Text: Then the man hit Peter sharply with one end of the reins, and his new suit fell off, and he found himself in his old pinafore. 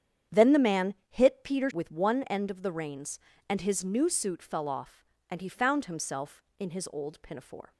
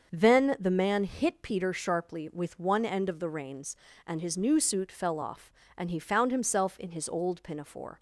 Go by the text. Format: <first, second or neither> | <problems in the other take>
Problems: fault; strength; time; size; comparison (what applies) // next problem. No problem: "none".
second | starts louder than the rest; strong; until 1.4 s; 9 dB; also in the second // pauses between "man" and "hit"; slight; at 0.9 s; 0.16 s long // skips "sharply"; at 1.6 s